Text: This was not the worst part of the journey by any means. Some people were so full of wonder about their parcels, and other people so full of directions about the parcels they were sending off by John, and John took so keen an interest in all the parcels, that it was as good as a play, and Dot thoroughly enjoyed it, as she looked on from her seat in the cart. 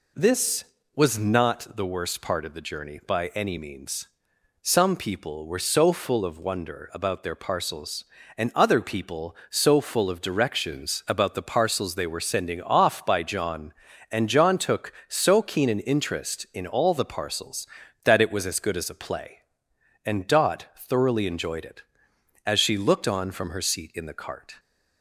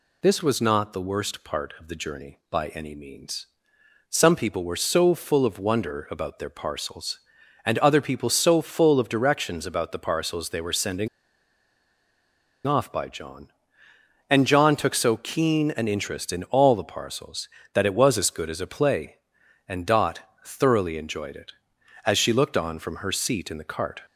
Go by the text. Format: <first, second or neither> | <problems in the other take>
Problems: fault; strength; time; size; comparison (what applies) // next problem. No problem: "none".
first | pauses between "sending" and "off"; strong; at 11.0 s; 1.5 s long // pauses between "Dot" and "thoroughly"; slight; at 20.1 s; 0.26 s long